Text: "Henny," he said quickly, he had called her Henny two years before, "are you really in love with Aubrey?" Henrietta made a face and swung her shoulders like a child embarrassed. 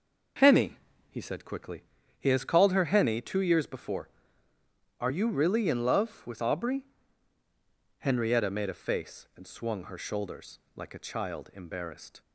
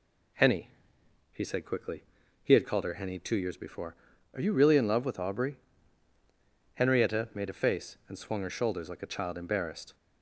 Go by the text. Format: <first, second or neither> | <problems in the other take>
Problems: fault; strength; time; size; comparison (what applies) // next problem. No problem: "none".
second | says "has" for "had"; at 2.2 s // pauses between "shoulders" and "like"; slight; at 10.5 s; 0.16 s long